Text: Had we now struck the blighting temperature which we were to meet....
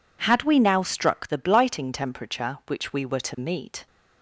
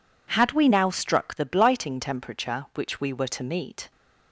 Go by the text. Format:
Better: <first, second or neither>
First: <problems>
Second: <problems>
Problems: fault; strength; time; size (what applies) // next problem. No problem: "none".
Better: neither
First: none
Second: none